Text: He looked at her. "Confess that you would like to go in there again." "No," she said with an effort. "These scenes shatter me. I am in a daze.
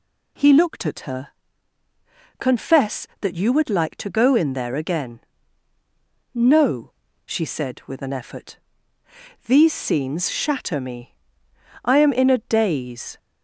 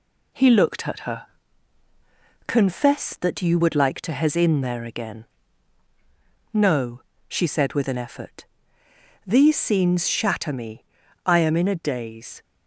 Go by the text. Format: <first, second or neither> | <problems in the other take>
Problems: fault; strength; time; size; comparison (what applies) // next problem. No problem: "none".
first | says "hez" for "go"; at 4.1 s